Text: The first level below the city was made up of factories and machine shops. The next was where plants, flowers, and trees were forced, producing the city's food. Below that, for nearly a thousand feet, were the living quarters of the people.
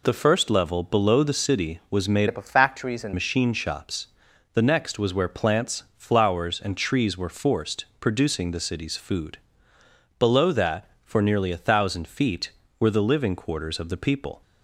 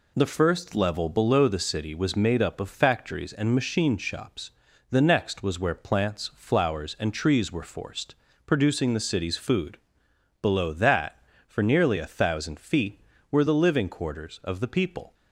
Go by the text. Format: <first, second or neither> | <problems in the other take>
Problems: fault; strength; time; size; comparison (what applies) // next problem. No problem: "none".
second | changes voice from "up" to "and"; from 2.2 to 3.1 s; 0.9 s long